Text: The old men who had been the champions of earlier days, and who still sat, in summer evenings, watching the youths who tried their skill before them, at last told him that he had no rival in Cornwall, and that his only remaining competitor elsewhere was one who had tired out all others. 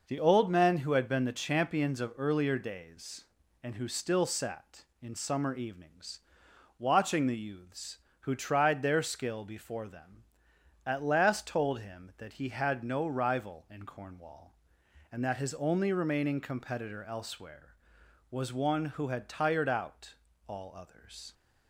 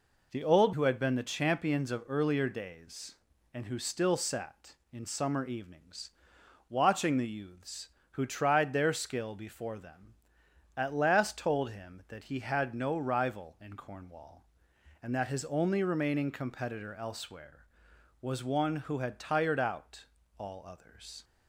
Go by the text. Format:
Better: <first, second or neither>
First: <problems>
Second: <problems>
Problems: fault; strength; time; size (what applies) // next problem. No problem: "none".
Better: first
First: pauses between "out" and "all"; slight; at 20.1 s; 0.32 s long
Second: skips "men"; at 0.7 s // pauses between "out" and "all"; slight; at 20.0 s; 0.32 s long